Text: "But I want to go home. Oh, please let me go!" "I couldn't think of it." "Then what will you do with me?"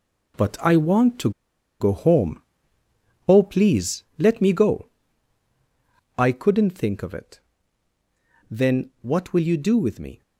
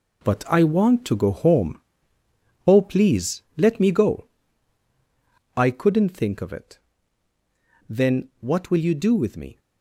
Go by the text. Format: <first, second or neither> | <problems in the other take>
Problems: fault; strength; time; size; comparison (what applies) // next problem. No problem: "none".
second | pauses between "to" and "go"; noticeable; at 1.3 s; 0.50 s long